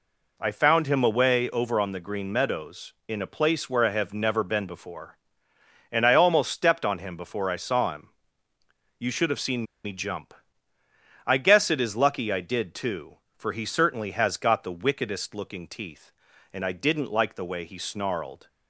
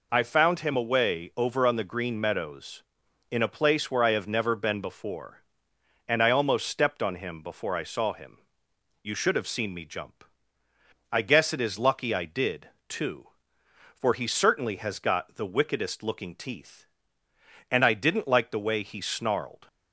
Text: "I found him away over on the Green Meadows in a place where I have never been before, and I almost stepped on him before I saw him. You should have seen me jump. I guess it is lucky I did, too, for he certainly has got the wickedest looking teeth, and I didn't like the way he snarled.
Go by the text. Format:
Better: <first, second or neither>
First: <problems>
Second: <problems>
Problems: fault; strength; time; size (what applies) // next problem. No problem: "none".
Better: second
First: pauses between "seen" and "me"; slight; at 9.6 s; 0.19 s long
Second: none